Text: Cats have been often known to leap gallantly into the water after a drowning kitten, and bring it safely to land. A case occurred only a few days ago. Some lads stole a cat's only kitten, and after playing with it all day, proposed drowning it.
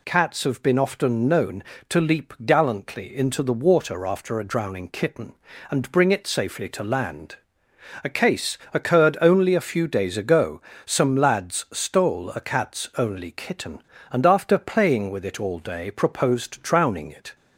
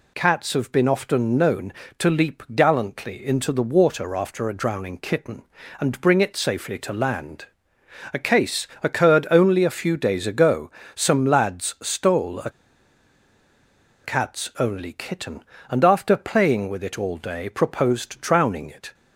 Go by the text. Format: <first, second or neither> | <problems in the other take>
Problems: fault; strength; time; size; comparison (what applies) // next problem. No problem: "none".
first | pauses between "case" and "occurred"; slight; at 8.6 s; 0.16 s long; slight in the first // pauses between "a" and "cat's"; strong; at 12.4 s; 1.5 s long